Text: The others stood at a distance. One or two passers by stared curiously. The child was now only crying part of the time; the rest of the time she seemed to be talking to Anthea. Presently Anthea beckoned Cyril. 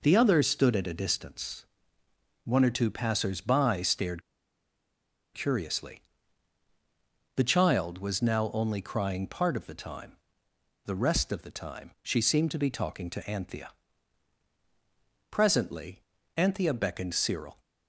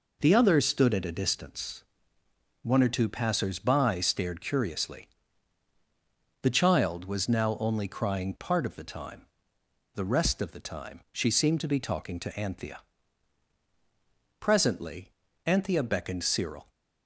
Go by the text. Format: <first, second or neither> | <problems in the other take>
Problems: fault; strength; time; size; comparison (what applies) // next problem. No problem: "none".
second | pauses between "stared" and "curiously"; at 4.2 s; 1.1 s long // pauses between "Presently" and "Anthea"; slight; at 16.0 s; 0.34 s long; slight in the second